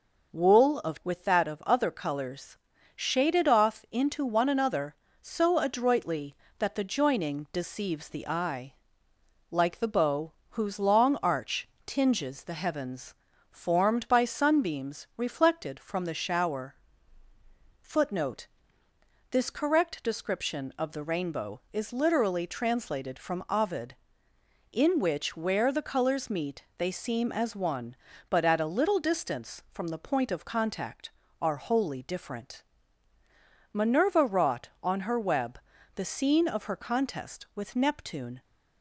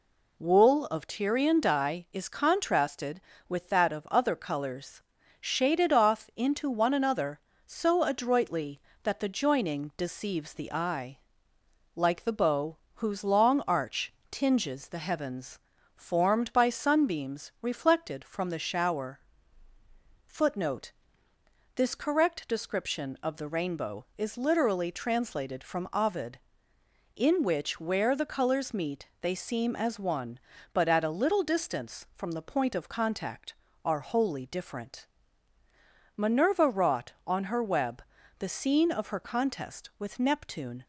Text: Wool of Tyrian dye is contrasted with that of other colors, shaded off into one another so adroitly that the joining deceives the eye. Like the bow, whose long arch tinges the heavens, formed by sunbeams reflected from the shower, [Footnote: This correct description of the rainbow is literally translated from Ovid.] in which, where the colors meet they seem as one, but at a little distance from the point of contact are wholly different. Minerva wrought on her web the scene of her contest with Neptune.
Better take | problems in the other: second | skips "Tyrian dye is contrasted"; at 1.0 s // pauses between "arch" and "tinges"; slight; at 11.6 s; 0.16 s long; slight in the second // pauses between "web" and "the"; at 35.5 s; 0.38 s long; also in the second

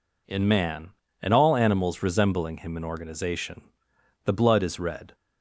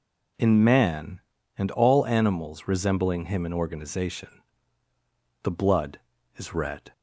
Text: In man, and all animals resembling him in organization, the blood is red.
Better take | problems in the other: neither | none

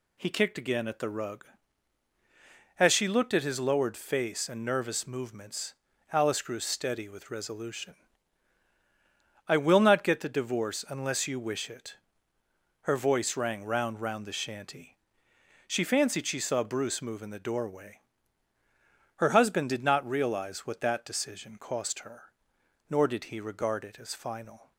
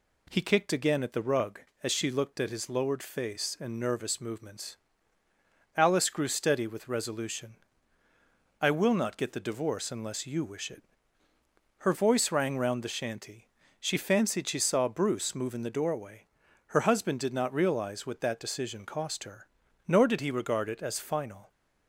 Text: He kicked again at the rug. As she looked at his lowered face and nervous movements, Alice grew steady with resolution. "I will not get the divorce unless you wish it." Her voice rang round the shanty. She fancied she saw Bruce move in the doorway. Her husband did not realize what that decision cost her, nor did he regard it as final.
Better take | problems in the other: second | says "round" twice; at 14.0 s

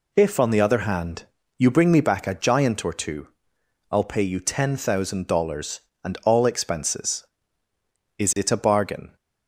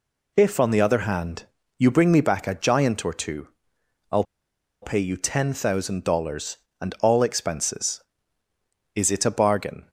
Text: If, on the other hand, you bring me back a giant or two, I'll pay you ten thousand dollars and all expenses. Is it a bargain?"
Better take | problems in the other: first | pauses between "I'll" and "pay"; noticeable; at 4.2 s; 0.59 s long

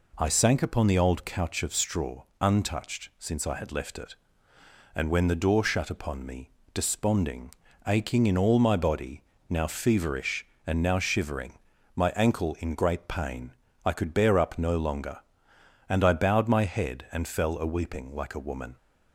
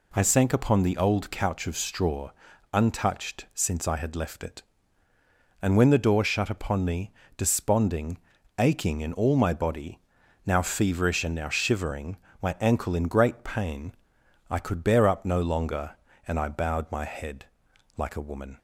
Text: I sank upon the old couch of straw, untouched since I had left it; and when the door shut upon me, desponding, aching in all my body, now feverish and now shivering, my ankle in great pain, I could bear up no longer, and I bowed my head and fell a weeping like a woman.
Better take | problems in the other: first | skips "and fell a weeping"; at 17.7 s

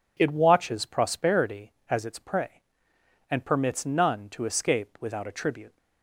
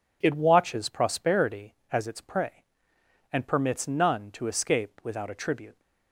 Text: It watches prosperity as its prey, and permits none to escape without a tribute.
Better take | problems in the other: neither | none

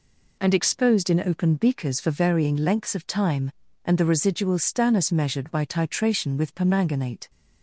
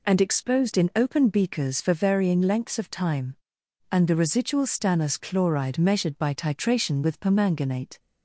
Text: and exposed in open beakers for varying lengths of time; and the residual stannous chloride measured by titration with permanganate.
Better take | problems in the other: second | skips "chloride"; at 5.1 s

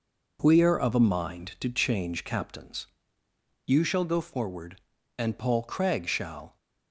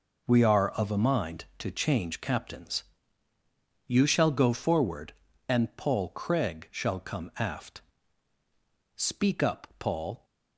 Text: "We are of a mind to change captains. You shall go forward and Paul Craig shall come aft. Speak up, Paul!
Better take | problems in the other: second | stops before "come aft Speak up Paul"; at 6.5 s

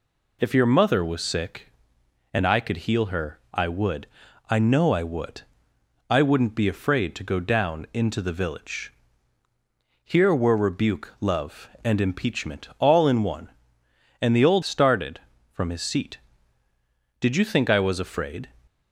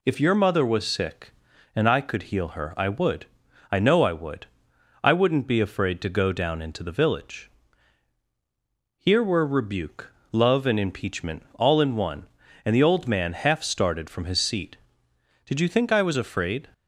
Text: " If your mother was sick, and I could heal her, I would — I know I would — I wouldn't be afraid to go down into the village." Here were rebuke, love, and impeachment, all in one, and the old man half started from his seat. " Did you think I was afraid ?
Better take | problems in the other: second | skips "man half"; at 14.6 s

